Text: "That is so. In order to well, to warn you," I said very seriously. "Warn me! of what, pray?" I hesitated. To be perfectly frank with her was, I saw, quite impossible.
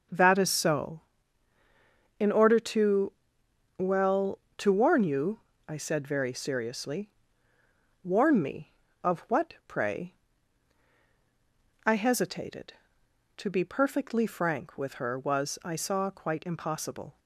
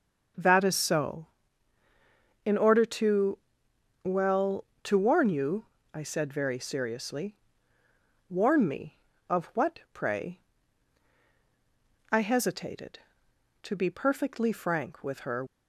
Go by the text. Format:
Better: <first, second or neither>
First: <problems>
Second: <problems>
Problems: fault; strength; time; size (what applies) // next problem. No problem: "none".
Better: first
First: pauses between "to" and "well"; noticeable; at 3.1 s; 0.64 s long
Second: pauses between "to" and "well"; noticeable; at 3.3 s; 0.64 s long // stops before "was I saw quite impossible"; at 15.4 s